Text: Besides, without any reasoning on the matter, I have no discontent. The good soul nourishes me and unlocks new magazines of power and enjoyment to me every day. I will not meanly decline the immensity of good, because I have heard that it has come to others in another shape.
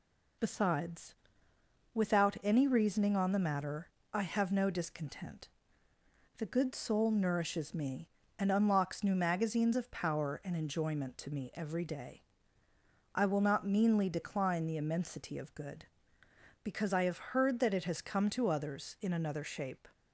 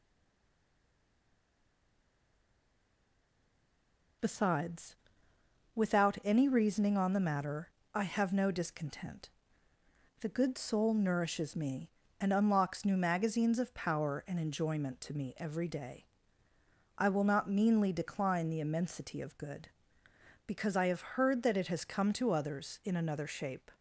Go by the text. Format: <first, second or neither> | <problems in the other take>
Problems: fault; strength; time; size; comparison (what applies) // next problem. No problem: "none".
first | stays silent before the first word; strong; until 4.2 s; 4.2 s long